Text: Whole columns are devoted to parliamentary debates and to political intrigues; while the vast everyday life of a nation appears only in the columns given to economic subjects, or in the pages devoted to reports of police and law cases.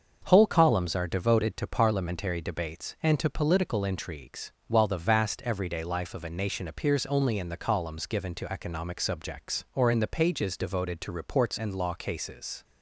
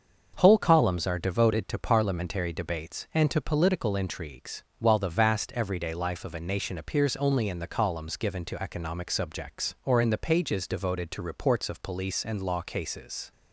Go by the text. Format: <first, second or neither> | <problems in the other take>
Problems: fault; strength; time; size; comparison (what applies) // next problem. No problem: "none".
second | starts louder than the rest; until 1.2 s; 6.5 dB; also in the second // skips "of police"; at 11.5 s